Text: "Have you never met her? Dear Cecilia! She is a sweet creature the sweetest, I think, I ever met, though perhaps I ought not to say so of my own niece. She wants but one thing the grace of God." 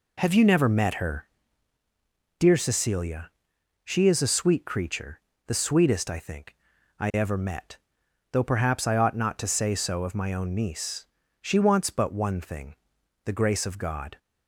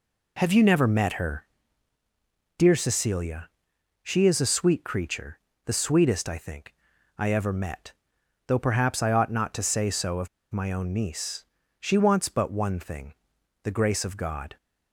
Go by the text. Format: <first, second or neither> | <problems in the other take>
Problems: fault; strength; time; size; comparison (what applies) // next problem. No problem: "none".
first | pauses between "creature" and "the"; slight; at 5.3 s; 0.26 s long; slight in the first // pauses between "of" and "my"; slight; at 10.2 s; 0.24 s long // pauses between "thing" and "the"; noticeable; at 13.1 s; 0.48 s long; noticeable in the first